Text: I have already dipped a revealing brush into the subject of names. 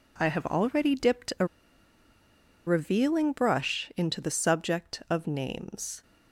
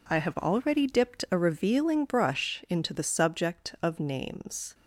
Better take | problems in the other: second | pauses between "a" and "revealing"; at 1.4 s; 1.2 s long

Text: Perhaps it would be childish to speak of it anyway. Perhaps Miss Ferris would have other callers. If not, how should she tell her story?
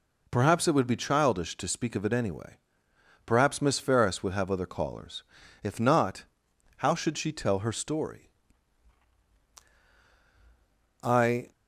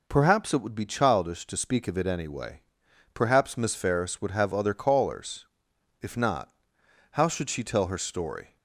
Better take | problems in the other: second | goes on to say "I"; slight; from 11.0 s on; 0.48 s long

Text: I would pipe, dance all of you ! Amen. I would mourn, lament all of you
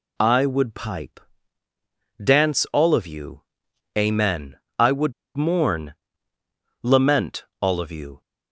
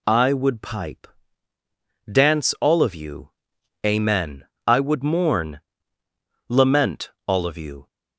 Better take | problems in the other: second | pauses between "would" and "mourn"; slight; at 5.1 s; 0.23 s long // pauses between "lament" and "all"; slight; at 7.4 s; 0.16 s long; slight in the second

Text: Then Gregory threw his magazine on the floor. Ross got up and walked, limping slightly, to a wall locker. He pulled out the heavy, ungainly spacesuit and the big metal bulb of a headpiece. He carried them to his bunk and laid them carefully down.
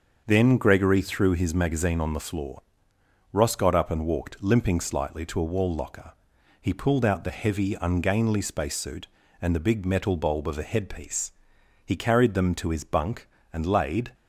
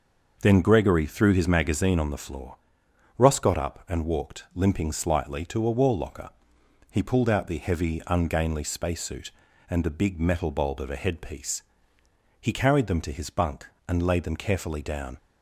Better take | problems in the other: second | starts louder than the rest; until 1.2 s; 6.5 dB; noticeable in the second // stops before "them carefully down"; at 14.1 s

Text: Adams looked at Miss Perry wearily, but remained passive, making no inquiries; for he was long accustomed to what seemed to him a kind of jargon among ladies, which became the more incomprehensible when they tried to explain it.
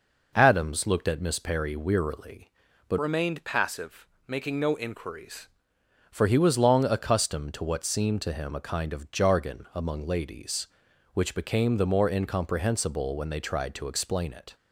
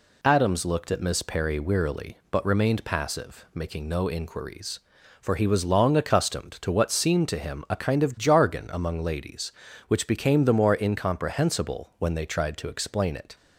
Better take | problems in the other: second | changes voice from "remained" to "inquiries"; from 2.9 to 5.4 s; 2.5 s long

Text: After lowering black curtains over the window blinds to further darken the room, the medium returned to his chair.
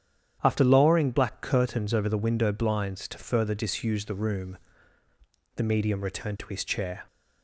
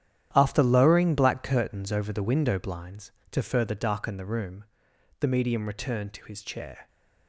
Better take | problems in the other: second | starts louder than the rest; strong; until 1.4 s; 9.5 dB; strong in the second // says "disuse" for "darken"; at 3.5 s

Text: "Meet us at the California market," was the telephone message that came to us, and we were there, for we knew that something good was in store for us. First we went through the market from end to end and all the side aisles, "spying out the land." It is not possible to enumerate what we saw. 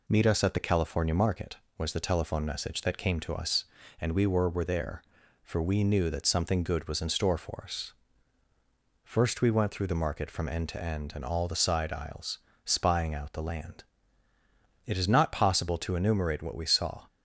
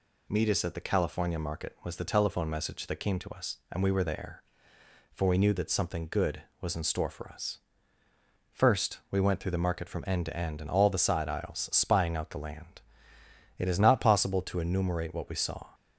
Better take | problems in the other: second | says "were" twice; at 4.4 s

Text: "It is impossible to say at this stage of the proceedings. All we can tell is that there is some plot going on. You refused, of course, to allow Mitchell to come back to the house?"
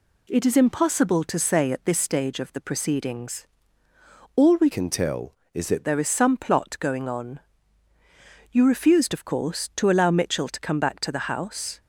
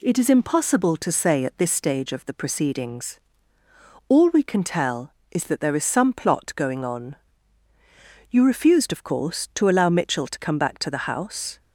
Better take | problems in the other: second | changes voice from "can" to "that"; from 4.7 to 5.8 s; 1.1 s long

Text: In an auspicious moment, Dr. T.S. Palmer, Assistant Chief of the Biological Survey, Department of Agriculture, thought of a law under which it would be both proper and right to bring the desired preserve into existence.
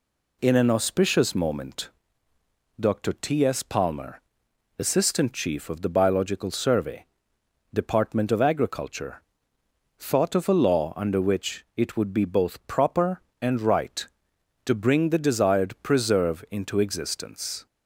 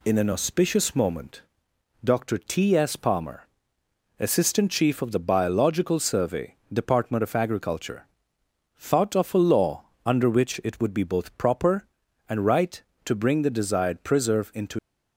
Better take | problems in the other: first | pauses between "law" and "under"; slight; at 9.8 s; 0.22 s long // stops before "existence"; at 14.7 s

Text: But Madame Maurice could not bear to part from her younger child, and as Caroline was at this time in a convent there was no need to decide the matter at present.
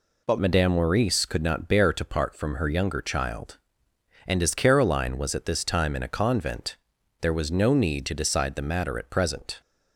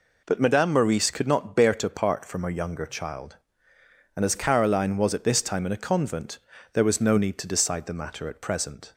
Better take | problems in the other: second | changes voice at "Madame"; from 0.3 s on; 9.3 s long // pauses between "convent" and "there"; at 6.7 s; 0.44 s long; slight in the second

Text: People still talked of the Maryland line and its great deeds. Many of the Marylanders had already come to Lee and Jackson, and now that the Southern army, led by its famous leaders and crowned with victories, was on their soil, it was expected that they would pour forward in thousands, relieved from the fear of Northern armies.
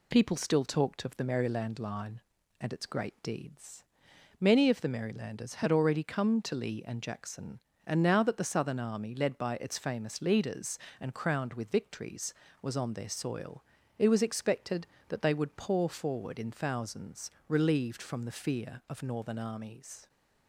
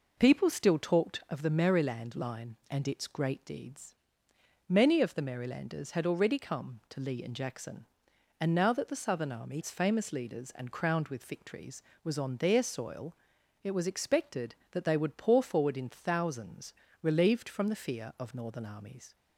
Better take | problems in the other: first | skips "led by"; at 9.6 s

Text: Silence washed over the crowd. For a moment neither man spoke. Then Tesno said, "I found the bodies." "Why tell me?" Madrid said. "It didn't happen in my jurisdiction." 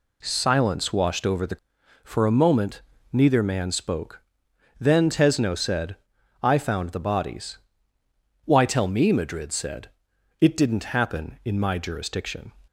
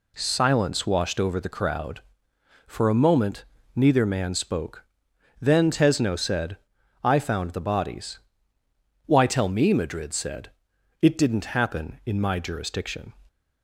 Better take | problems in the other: second | skips "crowd"; at 1.8 s // pauses between "moment" and "neither"; slight; at 2.8 s; 0.32 s long; slight in the second

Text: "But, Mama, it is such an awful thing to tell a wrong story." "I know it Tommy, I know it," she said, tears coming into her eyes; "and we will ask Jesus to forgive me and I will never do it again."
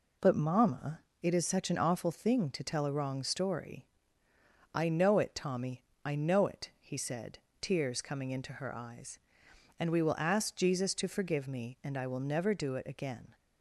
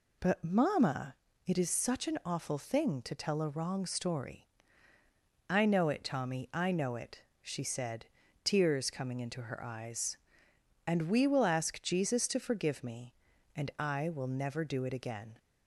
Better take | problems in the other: second | says "he" for "she"; at 6.8 s

